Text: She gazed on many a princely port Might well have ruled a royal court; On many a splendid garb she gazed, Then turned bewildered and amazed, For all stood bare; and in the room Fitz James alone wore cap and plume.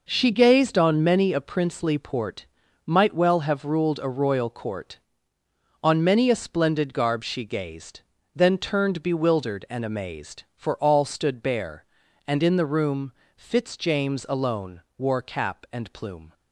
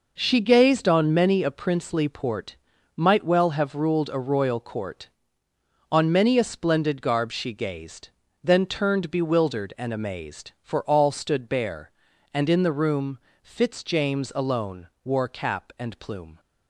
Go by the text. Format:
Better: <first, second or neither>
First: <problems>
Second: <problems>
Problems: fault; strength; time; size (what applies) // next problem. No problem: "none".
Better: neither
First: pauses between "port" and "Might"; at 2.4 s; 0.40 s long // pauses between "room" and "Fitz"; slight; at 13.1 s; 0.22 s long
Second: pauses between "port" and "Might"; at 2.5 s; 0.40 s long // pauses between "room" and "Fitz"; slight; at 13.1 s; 0.22 s long